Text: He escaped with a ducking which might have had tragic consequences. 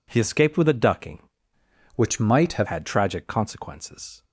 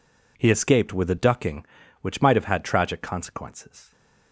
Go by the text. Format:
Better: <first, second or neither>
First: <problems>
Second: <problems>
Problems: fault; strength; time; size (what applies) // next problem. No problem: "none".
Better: second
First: changes voice from "which" to "have"; from 1.9 to 2.6 s; 0.7 s long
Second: none